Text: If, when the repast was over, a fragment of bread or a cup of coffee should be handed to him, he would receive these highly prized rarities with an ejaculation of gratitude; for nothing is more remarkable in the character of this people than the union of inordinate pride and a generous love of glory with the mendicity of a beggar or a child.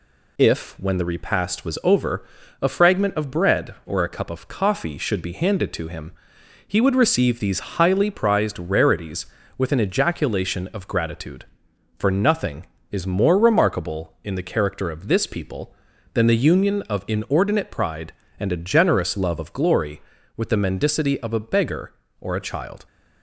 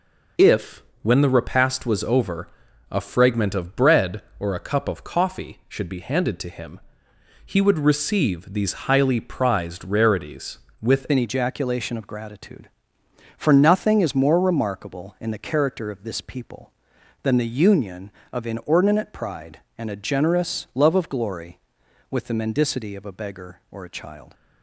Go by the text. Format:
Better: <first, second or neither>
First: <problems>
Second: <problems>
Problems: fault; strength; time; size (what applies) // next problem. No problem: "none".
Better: first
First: none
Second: changes voice at "an"; from 11.1 s on; 13.2 s long